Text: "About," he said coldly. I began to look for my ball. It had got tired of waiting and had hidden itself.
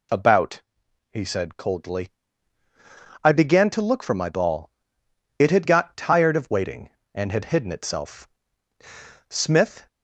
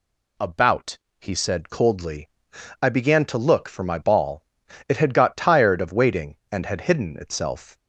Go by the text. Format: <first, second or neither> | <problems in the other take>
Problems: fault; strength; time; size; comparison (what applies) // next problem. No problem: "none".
second | goes on to say "Smith"; from 9.2 s on; 0.58 s long